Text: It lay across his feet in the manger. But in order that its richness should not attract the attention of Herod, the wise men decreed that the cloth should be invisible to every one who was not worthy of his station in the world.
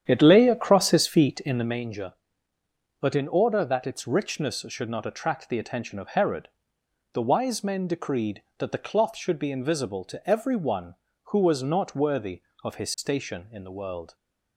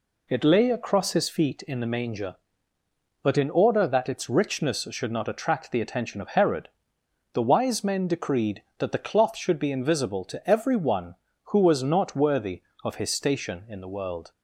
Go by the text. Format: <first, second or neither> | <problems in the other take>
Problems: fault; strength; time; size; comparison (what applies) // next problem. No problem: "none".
second | starts louder than the rest; strong; until 1.8 s; 9.5 dB